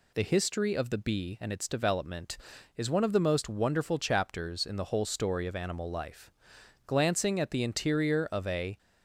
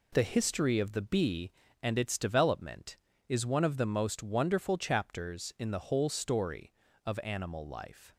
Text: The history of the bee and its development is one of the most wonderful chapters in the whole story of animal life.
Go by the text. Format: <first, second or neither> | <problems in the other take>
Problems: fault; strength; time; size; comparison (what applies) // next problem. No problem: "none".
second | goes on to say "Glancing at the interior of a"; strong; from 6.8 s on; 1.9 s long